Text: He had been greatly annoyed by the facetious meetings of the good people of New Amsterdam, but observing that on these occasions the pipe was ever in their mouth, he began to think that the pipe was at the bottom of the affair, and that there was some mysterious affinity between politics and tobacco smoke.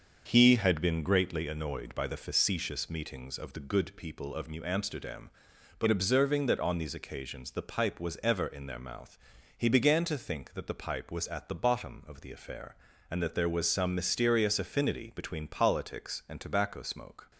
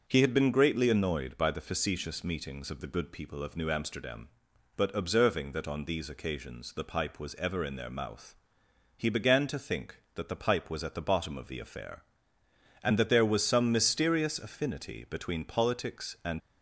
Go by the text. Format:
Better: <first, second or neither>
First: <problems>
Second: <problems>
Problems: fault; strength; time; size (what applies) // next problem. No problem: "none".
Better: first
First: starts louder than the rest; until 1.2 s; 6.5 dB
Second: starts louder than the rest; until 1.0 s; 6.5 dB // stops before "tobacco smoke"; at 16.3 s